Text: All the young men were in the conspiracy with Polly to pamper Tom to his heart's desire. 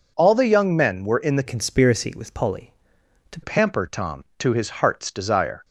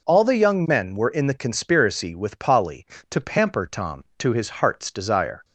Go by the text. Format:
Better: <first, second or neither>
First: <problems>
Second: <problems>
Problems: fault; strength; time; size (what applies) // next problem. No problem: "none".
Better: second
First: changes voice from "conspiracy" to "to"; from 1.4 to 3.3 s; 1.9 s long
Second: none